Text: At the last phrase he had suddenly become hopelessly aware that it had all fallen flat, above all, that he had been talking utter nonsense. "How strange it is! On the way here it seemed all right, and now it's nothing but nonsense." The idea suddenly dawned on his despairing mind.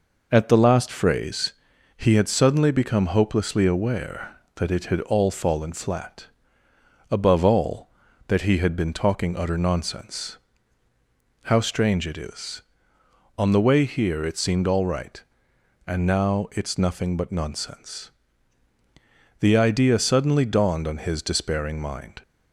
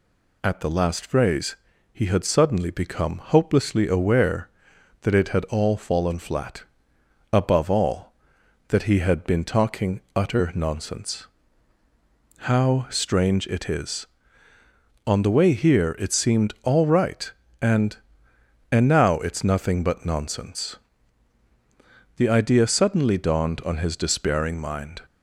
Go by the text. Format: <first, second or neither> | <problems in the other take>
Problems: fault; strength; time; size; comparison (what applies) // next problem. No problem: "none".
first | pauses between "phrase" and "he"; slight; at 1.5 s; 0.36 s long; also in the first // pauses between "talking" and "utter"; slight; at 9.9 s; 0.16 s long // says "and" twice; at 18.7 s